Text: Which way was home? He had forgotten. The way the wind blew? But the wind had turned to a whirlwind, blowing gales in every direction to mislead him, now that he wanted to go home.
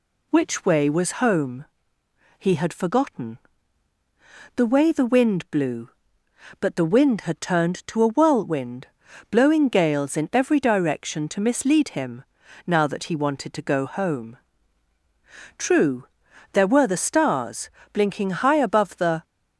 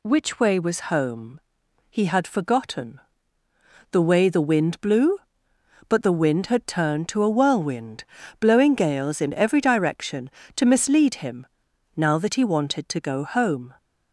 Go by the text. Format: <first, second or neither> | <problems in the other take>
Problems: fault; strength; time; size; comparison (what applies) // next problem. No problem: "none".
second | goes on to say "True there were the stars blinking high above the"; strong; from 15.5 s on; 3.6 s long